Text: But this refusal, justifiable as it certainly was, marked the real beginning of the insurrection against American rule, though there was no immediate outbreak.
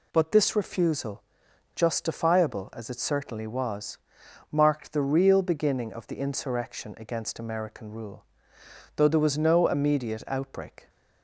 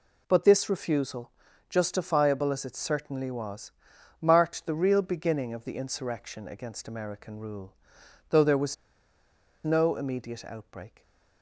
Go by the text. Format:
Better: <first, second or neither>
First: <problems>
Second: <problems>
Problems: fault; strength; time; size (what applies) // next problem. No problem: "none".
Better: first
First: none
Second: pauses between "was" and "no"; noticeable; at 8.7 s; 0.89 s long // stays silent after the last word; slight; from 10.8 s on; 0.6 s long